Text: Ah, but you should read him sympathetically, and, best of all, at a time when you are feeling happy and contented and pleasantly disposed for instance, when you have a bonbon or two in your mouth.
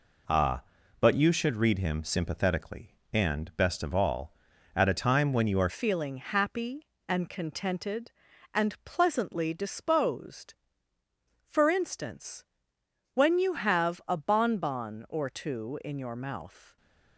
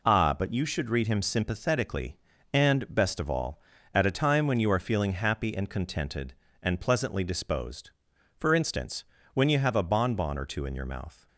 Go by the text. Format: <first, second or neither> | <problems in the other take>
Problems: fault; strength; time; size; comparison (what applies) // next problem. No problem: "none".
second | changes voice at "feeling"; from 5.6 s on; 11.1 s long